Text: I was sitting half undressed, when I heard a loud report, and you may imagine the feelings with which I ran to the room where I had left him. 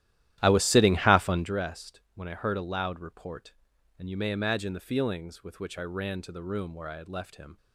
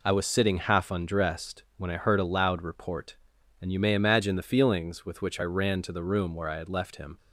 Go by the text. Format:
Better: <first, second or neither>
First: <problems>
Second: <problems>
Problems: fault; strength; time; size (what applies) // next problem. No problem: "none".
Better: second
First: starts louder than the rest; strong; until 1.6 s; 13 dB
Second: none